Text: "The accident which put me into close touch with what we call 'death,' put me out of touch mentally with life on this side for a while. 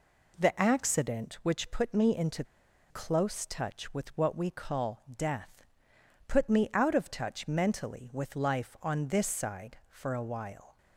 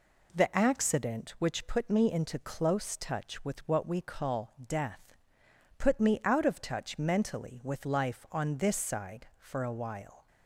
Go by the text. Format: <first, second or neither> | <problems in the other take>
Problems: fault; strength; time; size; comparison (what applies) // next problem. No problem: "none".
second | pauses between "into" and "close"; noticeable; at 2.4 s; 0.46 s long